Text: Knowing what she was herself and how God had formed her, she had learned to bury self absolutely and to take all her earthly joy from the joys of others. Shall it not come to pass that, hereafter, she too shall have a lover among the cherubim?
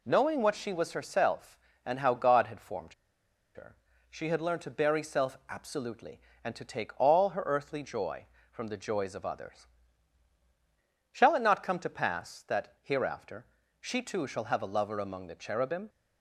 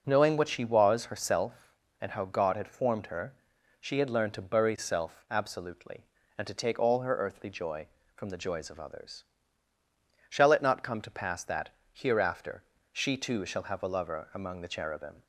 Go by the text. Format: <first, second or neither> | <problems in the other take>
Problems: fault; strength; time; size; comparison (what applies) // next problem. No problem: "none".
second | pauses between "formed" and "her"; noticeable; at 2.9 s; 0.60 s long